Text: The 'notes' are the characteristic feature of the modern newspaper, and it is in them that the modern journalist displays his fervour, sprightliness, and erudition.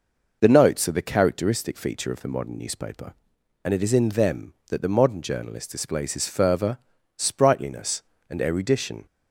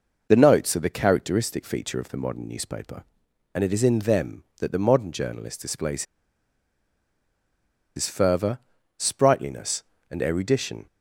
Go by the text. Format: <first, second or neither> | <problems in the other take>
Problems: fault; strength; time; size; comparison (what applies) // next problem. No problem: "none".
first | pauses between "displays" and "his"; strong; at 6.0 s; 1.9 s long